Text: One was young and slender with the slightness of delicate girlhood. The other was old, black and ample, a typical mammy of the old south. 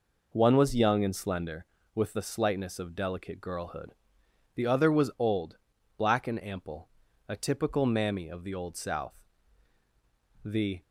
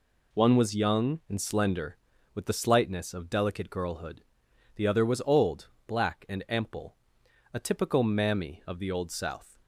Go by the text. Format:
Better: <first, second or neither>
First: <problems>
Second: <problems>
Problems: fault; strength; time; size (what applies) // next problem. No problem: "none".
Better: second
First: goes on to say "The"; slight; from 10.4 s on; 0.40 s long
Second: none